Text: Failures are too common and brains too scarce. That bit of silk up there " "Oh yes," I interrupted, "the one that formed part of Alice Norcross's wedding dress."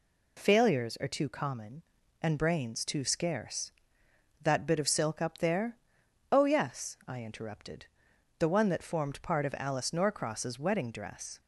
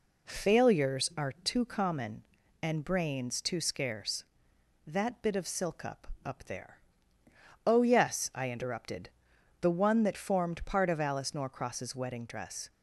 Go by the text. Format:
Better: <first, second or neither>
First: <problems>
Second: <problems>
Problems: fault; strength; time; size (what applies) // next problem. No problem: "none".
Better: first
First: none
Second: says "up" twice; at 6.2 s